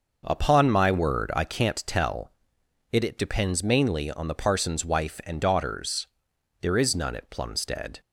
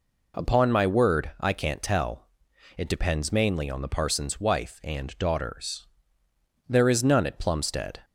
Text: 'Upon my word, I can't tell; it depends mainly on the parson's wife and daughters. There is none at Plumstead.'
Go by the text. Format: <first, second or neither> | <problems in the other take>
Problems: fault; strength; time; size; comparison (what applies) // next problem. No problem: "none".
second | says "it" twice; at 3.0 s